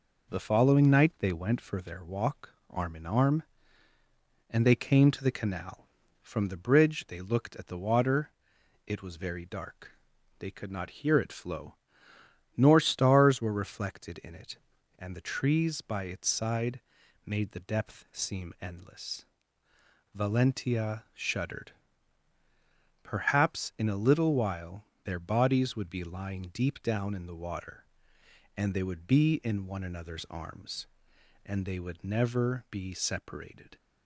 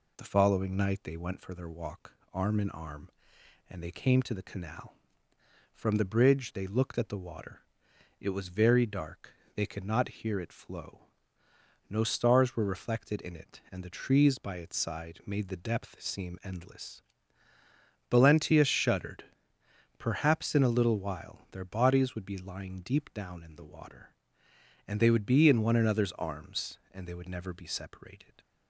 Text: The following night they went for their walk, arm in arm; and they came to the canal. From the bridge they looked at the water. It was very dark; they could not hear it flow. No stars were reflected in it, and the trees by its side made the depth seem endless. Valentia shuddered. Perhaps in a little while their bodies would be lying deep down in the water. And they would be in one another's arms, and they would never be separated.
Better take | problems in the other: second | says "Nor" for "No"; at 12.5 s // pauses between "side" and "made"; noticeable; at 16.7 s; 0.46 s long // pauses between "while" and "their"; slight; at 24.8 s; 0.22 s long

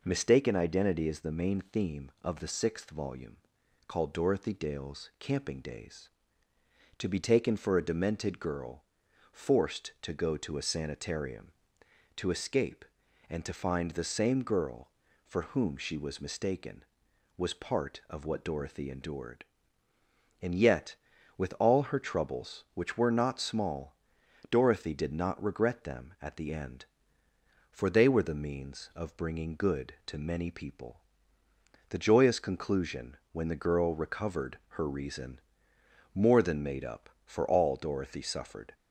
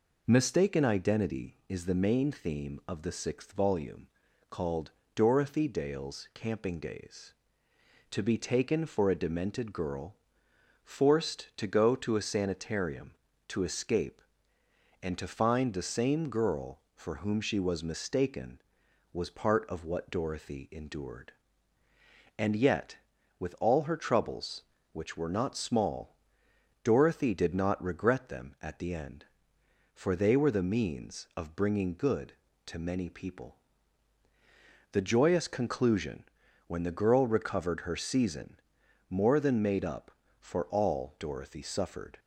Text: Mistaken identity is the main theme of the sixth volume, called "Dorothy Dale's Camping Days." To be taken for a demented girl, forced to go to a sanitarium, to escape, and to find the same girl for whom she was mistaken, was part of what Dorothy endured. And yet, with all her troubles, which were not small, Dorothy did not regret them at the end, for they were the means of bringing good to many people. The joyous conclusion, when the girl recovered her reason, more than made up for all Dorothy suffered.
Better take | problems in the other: first | pauses between "called" and "Dorothy"; slight; at 4.9 s; 0.24 s long // says "season" for "reason"; at 37.9 s

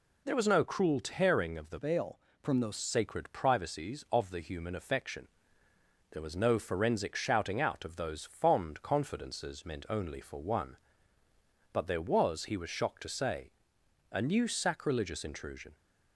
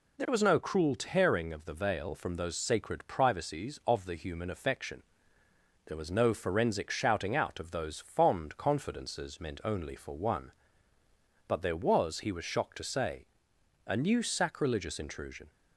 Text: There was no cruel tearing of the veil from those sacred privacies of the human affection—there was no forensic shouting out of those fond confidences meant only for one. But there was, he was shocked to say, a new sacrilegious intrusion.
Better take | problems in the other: second | changes voice from "veil" to "those"; from 1.7 to 2.7 s; 1.0 s long

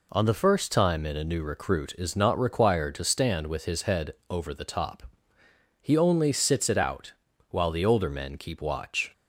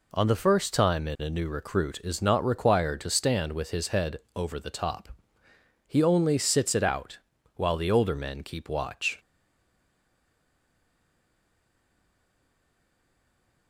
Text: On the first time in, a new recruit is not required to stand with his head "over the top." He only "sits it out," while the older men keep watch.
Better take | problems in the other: first | pauses between "head" and "over"; slight; at 4.2 s; 0.16 s long; slight in the first // stays silent after the last word; strong; from 9.1 s on; 4.5 s long

